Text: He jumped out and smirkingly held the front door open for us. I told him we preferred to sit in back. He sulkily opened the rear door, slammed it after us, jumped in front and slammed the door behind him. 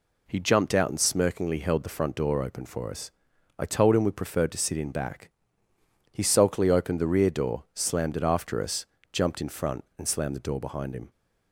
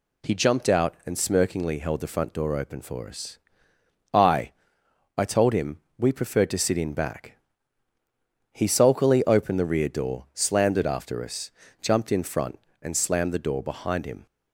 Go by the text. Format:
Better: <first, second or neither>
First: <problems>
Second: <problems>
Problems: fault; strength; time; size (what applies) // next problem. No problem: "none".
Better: first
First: none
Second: says "I" twice; at 5.1 s // pauses between "him" and "we"; slight; at 5.7 s; 0.20 s long